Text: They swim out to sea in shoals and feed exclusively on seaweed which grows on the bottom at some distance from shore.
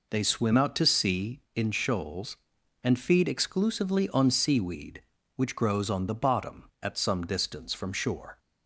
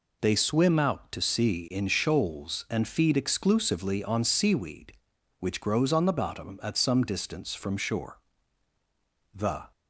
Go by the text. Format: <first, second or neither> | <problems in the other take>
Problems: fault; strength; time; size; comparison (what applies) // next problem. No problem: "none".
first | goes on to say "The"; slight; from 9.3 s on; 0.38 s long